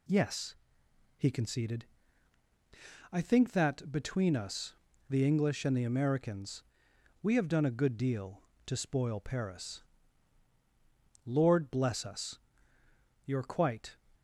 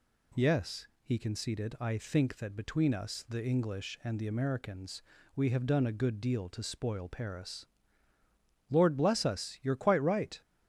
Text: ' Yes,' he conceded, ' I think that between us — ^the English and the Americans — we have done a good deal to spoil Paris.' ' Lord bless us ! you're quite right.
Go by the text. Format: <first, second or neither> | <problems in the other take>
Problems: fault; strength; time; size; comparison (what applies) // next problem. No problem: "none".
second | stops before "right"; at 14.1 s